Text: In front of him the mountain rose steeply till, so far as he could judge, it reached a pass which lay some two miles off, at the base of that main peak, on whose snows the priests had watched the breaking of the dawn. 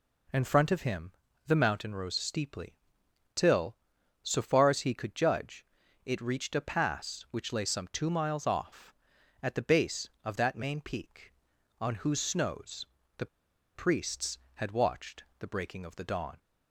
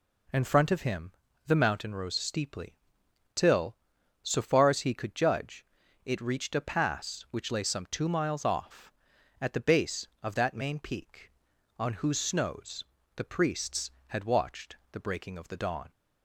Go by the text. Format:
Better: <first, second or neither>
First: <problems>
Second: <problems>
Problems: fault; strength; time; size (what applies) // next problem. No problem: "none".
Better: second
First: pauses between "him" and "the"; slight; at 1.1 s; 0.34 s long // pauses between "steeply" and "till"; noticeable; at 2.7 s; 0.58 s long // pauses between "snows" and "the"; slight; at 12.8 s; 0.32 s long // pauses between "the" and "priests"; noticeable; at 13.2 s; 0.48 s long // pauses between "watched" and "the"; slight; at 15.2 s; 0.16 s long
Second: pauses between "him" and "the"; slight; at 1.1 s; 0.34 s long // pauses between "steeply" and "till"; noticeable; at 2.7 s; 0.58 s long // pauses between "snows" and "the"; slight; at 12.8 s; 0.32 s long // pauses between "watched" and "the"; slight; at 14.7 s; 0.16 s long